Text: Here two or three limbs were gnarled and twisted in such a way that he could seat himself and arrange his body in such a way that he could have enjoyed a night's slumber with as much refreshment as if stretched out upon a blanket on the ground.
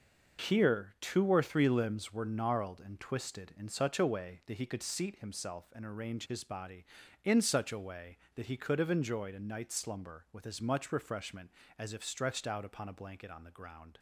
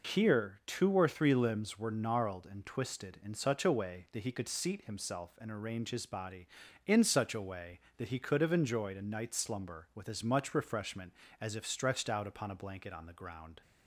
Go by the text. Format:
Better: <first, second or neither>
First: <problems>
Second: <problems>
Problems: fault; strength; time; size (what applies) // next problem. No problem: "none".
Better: second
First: gets quieter; strong; throughout; 9 dB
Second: none